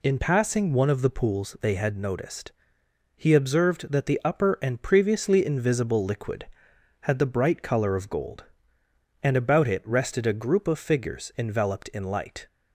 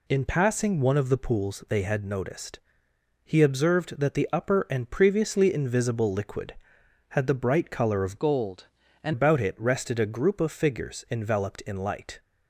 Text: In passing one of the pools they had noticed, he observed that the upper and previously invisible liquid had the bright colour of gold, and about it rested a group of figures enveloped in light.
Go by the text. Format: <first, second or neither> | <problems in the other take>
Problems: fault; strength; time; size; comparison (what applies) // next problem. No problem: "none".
first | changes voice from "gold" to "and"; from 8.1 to 9.1 s; 1.0 s long